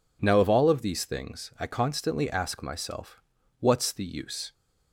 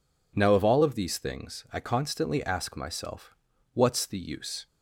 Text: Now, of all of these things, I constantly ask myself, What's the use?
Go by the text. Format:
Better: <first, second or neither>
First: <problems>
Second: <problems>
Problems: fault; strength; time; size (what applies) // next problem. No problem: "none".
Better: neither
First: none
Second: none